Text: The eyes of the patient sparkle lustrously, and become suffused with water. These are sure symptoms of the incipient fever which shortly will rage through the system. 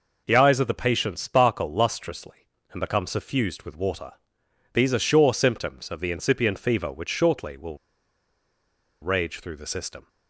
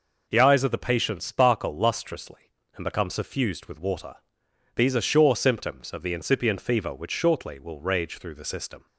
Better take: second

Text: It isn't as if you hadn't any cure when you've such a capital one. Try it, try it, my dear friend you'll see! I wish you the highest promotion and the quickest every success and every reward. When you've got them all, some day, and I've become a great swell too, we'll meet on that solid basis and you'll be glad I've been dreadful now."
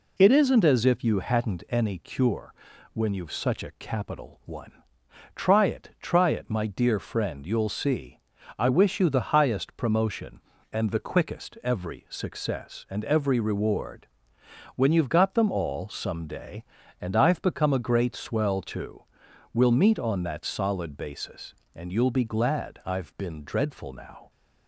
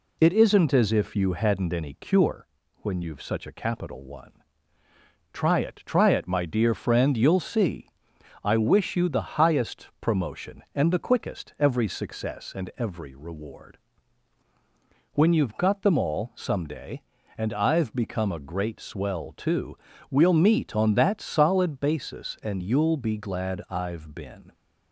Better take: first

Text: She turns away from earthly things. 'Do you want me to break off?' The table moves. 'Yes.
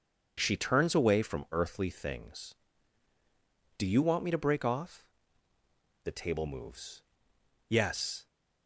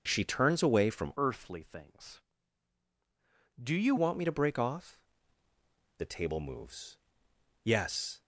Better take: first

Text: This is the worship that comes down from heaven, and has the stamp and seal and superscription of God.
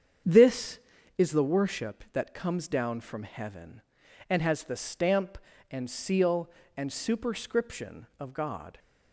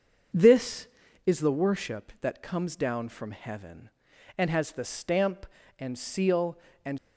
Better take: first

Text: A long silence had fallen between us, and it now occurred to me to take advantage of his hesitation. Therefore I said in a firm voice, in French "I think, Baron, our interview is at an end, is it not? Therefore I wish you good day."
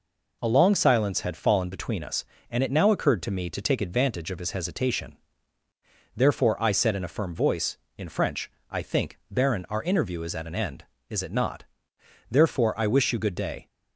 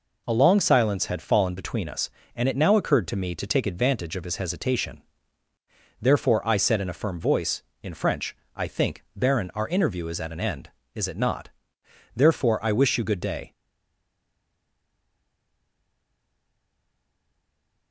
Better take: first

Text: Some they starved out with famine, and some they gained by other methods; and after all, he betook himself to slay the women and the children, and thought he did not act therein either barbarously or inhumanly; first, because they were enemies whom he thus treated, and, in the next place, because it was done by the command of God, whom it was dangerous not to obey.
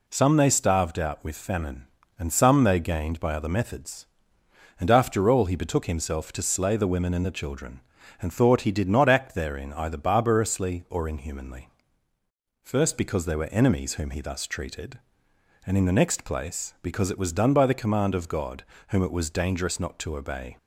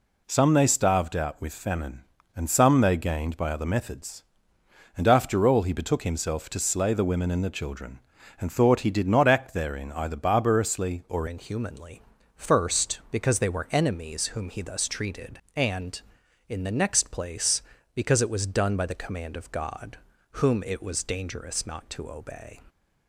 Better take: first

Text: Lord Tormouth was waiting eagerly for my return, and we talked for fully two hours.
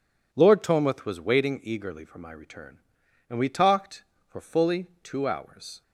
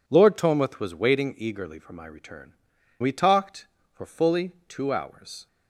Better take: first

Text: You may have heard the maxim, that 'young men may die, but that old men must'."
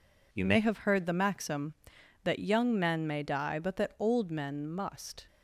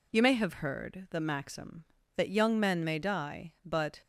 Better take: first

